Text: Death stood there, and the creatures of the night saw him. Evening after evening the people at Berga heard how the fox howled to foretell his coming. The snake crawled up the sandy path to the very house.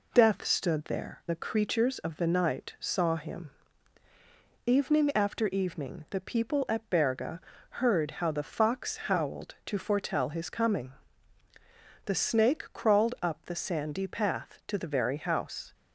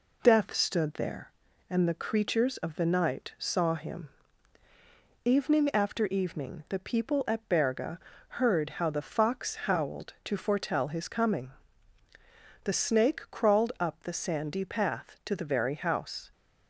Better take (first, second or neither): second